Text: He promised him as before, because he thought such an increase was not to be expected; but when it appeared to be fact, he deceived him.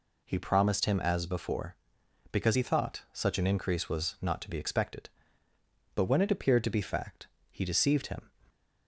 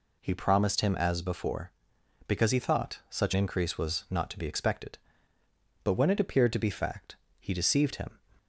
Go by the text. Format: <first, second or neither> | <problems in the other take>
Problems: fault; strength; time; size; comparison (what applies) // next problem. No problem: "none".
first | skips "an"; at 3.3 s